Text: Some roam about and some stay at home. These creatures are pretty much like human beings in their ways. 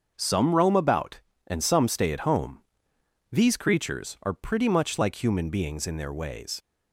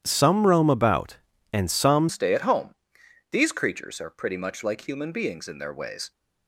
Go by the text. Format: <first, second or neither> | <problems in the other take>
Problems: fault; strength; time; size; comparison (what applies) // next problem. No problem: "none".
first | starts louder than the rest; strong; until 1.0 s; 11 dB; also in the first // changes voice at "stay"; from 2.0 s on; 4.1 s long